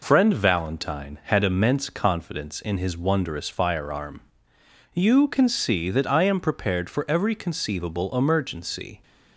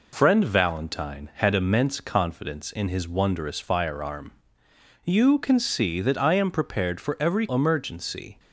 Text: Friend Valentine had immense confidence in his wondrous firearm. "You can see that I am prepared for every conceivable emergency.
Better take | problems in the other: first | skips "conceivable"; at 7.4 s

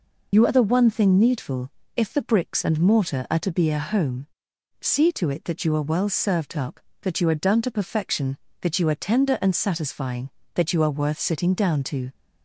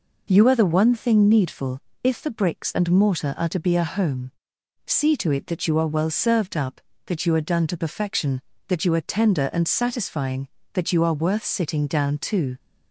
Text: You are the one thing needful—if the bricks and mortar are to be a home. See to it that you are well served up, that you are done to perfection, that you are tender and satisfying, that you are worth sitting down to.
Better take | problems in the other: second | loses the start of "You"; at 0.3 s; 60 ms

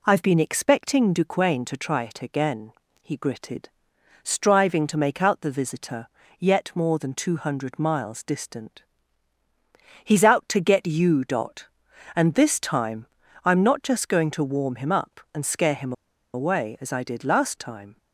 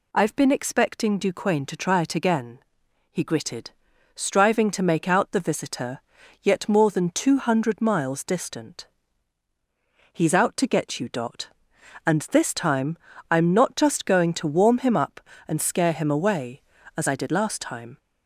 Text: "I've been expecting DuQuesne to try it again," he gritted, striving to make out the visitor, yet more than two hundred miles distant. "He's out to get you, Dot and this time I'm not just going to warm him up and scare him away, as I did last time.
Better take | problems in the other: second | pauses between "time" and "I'm"; at 13.0 s; 0.38 s long; slight in the second // pauses between "him" and "away"; at 15.9 s; 0.41 s long

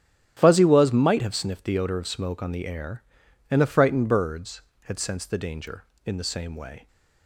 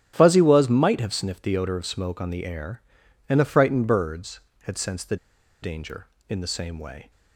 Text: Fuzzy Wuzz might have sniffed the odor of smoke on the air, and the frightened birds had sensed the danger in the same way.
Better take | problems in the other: first | starts louder than the rest; strong; until 1.1 s; 11 dB; strong in the first // pauses between "the" and "danger"; at 5.1 s; 0.45 s long

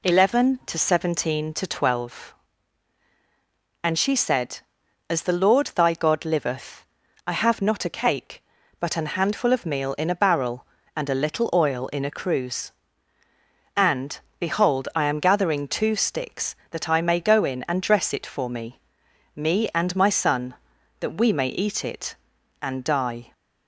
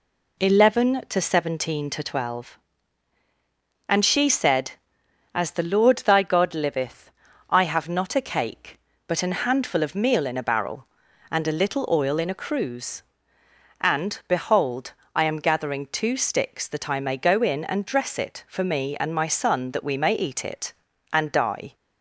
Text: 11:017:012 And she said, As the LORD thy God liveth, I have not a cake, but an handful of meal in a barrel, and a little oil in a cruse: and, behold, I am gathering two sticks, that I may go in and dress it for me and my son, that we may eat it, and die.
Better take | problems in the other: second | says "me" twice; at 19.3 s

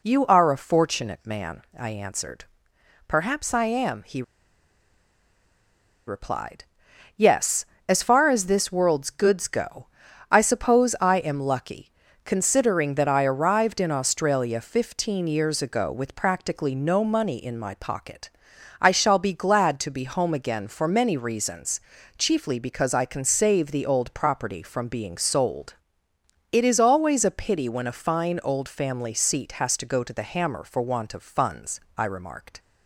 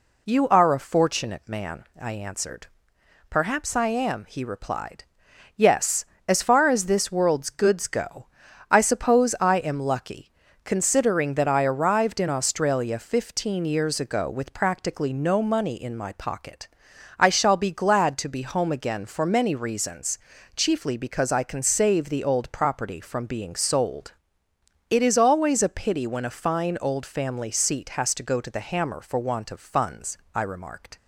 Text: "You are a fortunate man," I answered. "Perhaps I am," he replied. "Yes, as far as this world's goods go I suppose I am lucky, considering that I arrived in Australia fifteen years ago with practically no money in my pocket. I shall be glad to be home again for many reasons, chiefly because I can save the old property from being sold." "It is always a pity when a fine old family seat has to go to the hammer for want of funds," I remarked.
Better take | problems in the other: second | pauses between "he" and "replied"; strong; at 4.2 s; 1.8 s long // pauses between "go" and "I"; at 9.8 s; 0.44 s long; also in the second

